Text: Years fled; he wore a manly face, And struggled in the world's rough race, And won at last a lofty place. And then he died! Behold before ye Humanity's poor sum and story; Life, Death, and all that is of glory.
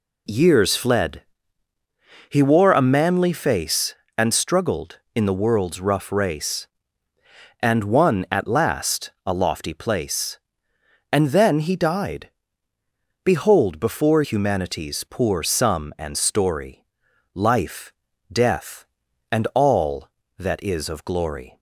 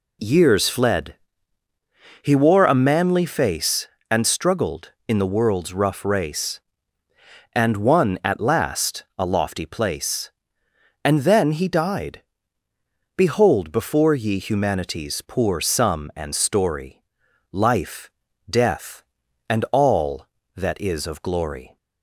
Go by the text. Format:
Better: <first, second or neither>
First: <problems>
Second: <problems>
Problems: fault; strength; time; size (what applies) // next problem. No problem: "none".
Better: second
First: skips "ye"; at 14.2 s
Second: none